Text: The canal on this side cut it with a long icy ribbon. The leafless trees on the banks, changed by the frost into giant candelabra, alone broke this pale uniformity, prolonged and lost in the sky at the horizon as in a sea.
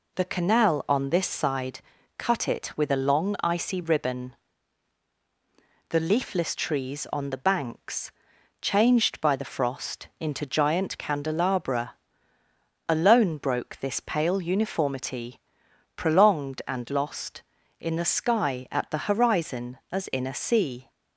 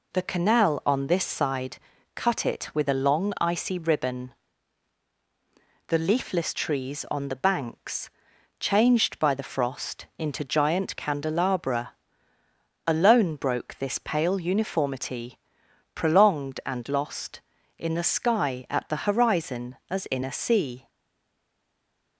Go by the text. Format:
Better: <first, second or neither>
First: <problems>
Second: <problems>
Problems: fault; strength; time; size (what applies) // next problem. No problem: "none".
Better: first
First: pauses between "side" and "cut"; at 1.7 s; 0.38 s long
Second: pauses between "side" and "cut"; at 1.7 s; 0.38 s long // stays silent after the last word; noticeable; from 20.8 s on; 1.3 s long